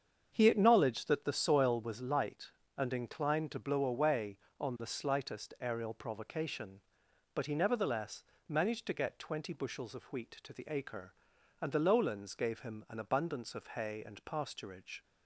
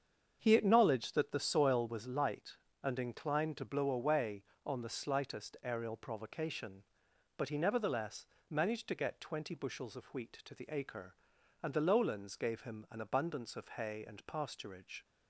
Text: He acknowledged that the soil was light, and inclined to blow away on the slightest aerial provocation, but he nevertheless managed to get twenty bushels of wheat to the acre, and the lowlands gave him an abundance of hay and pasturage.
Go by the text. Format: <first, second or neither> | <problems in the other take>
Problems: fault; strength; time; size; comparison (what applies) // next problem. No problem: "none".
neither | starts louder than the rest; strong; the same in both // pauses between "nevertheless" and "managed"; slight; the same in both